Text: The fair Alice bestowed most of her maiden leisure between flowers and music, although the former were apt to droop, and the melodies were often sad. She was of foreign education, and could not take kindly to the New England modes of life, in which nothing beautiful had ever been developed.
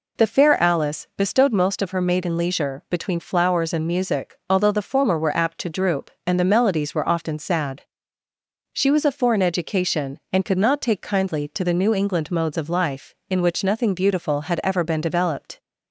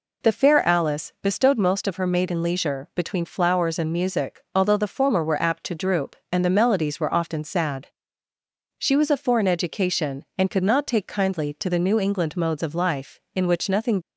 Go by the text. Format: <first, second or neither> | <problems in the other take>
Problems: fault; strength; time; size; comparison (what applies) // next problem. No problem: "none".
first | stops before "beautiful had ever been developed"; at 14.0 s